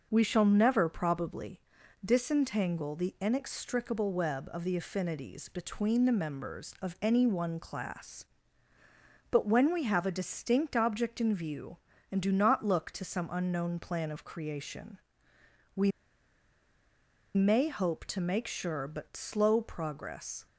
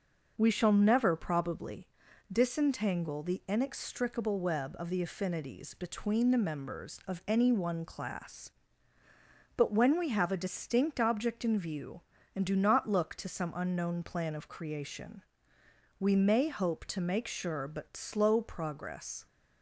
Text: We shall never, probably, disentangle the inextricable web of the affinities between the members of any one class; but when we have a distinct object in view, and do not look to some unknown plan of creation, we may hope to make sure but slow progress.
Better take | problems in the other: second | starts louder than the rest; noticeable; until 1.1 s; 6 dB // pauses between "we" and "may"; strong; at 15.9 s; 1.4 s long

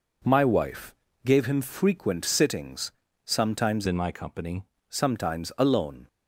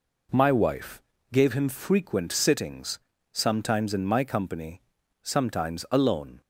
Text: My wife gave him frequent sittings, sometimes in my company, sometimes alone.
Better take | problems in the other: second | pauses between "wife" and "gave"; slight; at 0.9 s; 0.30 s long; slight in the second // changes voice from "in" to "company"; from 3.8 to 4.6 s; 0.8 s long

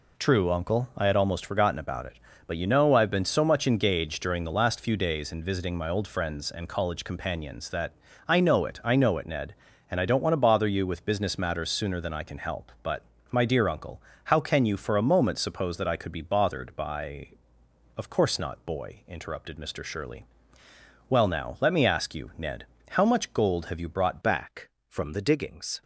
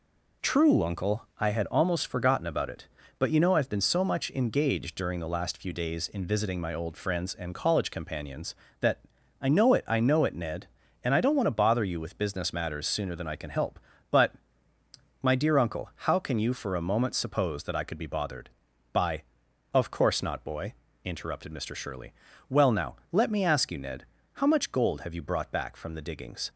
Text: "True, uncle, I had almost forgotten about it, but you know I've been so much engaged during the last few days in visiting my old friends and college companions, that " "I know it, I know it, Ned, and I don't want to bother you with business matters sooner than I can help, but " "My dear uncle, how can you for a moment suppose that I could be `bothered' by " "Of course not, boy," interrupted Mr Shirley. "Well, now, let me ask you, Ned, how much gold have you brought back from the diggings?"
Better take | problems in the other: second | changes voice at "back"; from 24.2 s on; 1.6 s long

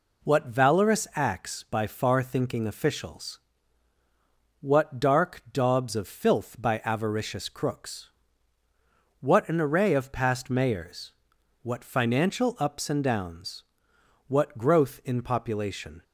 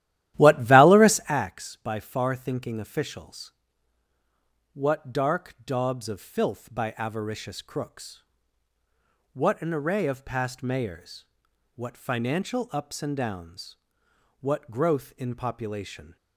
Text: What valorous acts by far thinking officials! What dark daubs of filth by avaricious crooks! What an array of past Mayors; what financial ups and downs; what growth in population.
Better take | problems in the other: first | starts louder than the rest; strong; until 1.5 s; 13.5 dB

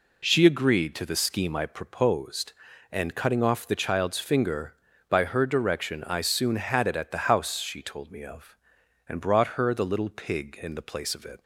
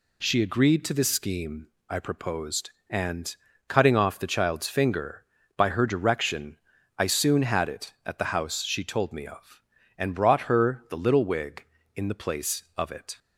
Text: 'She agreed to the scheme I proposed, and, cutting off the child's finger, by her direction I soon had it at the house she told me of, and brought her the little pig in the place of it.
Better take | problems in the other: first | pauses between "scheme" and "I"; slight; at 1.6 s; 0.24 s long // pauses between "direction" and "I"; slight; at 6.5 s; 0.36 s long // says "wig" for "pig"; at 11.2 s

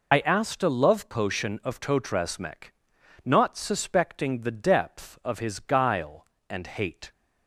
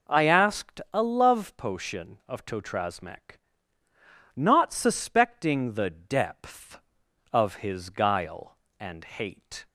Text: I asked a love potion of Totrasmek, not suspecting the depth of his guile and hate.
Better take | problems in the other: second | loses the start of "I"; at 0.1 s; 65 ms

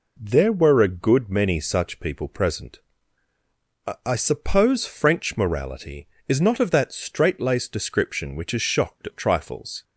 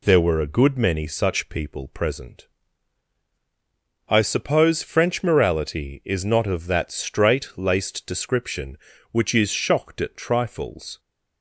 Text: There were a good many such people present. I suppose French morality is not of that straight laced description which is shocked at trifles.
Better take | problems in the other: second | says "I" twice; at 4.0 s

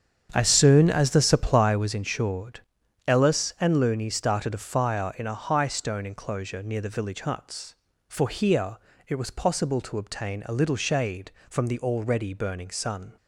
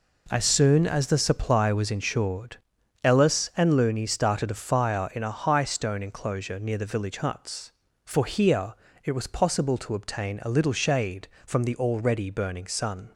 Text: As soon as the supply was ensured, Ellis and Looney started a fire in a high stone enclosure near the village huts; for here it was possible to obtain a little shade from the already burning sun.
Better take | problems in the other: second | starts louder than the rest; strong; until 1.8 s; 7.5 dB // pauses between "here" and "it"; slight; at 8.7 s; 0.32 s long; slight in the second

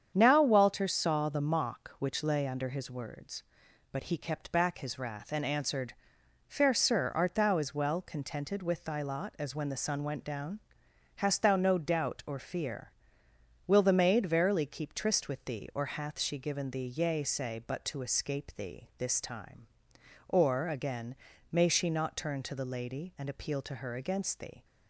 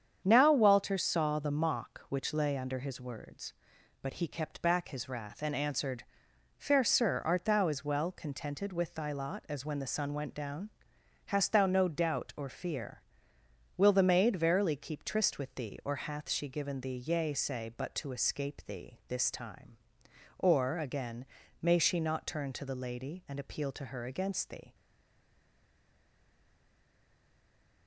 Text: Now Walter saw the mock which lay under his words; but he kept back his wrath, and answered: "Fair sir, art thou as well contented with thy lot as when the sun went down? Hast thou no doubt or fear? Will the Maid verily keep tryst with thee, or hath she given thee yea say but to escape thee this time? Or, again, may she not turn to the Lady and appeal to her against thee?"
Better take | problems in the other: first | starts louder than the rest; strong; until 1.2 s; 8 dB; strong in the first // stays silent after the last word; strong; from 24.7 s on; 3.1 s long

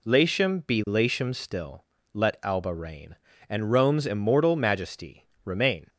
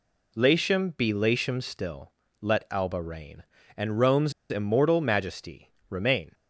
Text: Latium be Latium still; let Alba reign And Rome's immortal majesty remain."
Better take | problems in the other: first | pauses between "Rome's" and "immortal"; slight; at 4.3 s; 0.17 s long // pauses between "majesty" and "remain"; slight; at 5.6 s; 0.20 s long; slight in the first

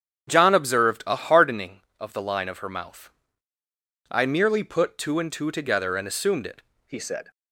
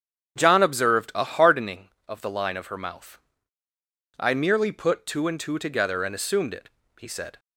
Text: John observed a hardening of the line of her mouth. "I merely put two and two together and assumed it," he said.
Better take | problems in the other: second | starts louder than the rest; strong; until 1.3 s; 8.5 dB; strong in the second // changes voice at "he"; from 6.8 s on; 0.5 s long

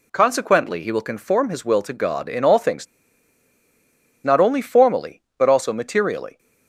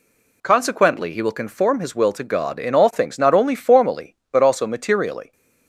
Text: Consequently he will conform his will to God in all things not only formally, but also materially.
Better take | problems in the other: second | pauses between "things" and "not"; strong; at 2.8 s; 1.3 s long

